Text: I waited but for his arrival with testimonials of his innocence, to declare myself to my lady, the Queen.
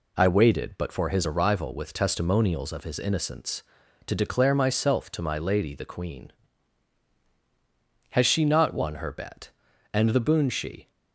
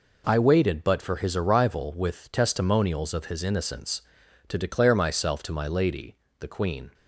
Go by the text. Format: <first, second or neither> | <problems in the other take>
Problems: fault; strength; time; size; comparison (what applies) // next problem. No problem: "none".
second | goes on to say "Has she not won her bet And the boon she"; strong; from 8.1 s on; 2.8 s long